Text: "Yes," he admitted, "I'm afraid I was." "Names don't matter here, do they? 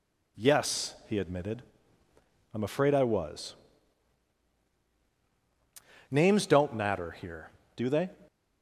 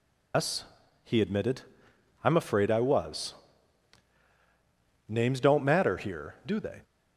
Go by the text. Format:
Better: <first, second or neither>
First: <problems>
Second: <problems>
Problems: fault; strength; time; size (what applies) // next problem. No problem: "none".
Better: first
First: none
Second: loses the start of "Yes"; at 0.3 s; 165 ms